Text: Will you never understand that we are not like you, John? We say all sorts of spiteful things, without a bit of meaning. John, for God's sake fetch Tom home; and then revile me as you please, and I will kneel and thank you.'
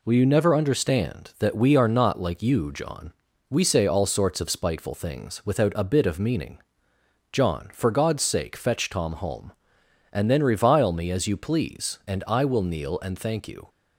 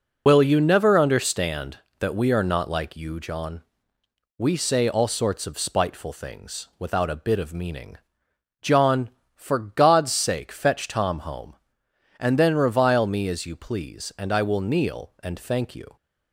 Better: first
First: none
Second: loses the start of "Will"; at 0.2 s; 105 ms

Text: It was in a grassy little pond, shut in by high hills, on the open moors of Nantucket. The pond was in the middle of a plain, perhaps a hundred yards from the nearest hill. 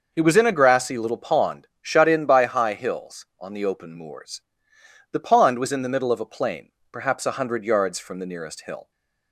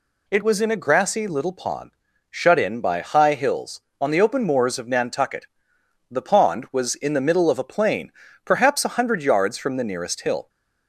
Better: second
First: skips "of Nantucket"; at 4.7 s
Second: none

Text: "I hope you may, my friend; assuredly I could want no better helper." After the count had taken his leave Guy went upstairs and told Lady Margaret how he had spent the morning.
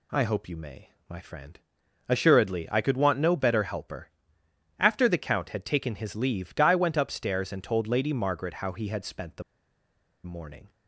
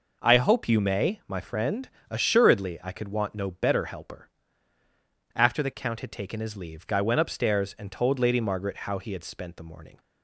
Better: second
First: pauses between "the" and "morning"; noticeable; at 9.4 s; 0.81 s long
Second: none

